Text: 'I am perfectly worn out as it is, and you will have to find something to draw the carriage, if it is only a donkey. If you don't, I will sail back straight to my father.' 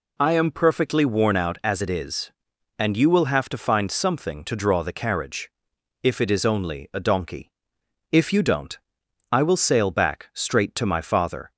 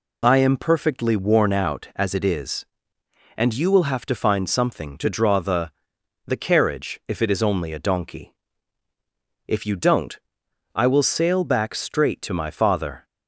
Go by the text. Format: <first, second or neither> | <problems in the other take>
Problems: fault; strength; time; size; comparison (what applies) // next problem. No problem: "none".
first | says "the" twice; at 6.2 s